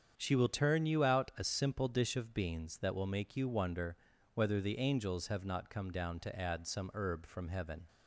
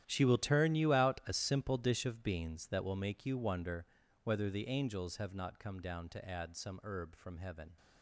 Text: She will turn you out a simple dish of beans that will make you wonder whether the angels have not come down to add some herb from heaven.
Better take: first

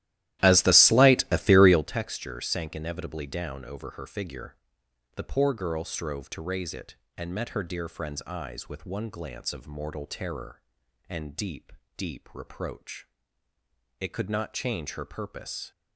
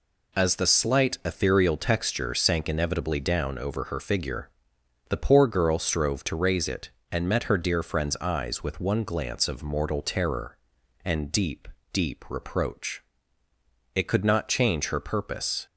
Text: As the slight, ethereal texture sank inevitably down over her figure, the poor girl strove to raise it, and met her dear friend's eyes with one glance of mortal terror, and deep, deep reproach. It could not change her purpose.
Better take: second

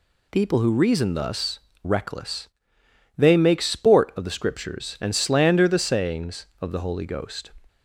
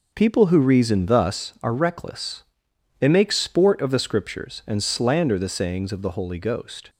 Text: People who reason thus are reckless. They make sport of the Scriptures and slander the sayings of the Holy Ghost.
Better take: second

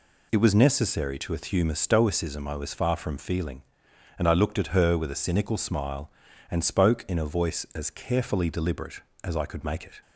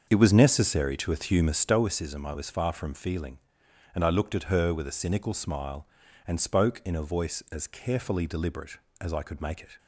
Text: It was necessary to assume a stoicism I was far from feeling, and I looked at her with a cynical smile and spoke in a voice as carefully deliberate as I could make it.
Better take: first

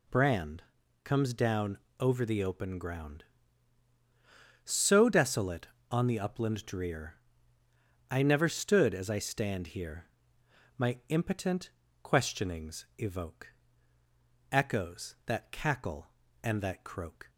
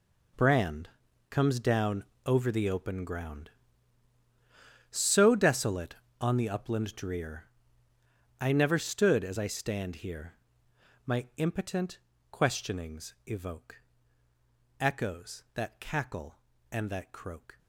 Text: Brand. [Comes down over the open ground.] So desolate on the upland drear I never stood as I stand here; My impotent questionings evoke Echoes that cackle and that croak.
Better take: first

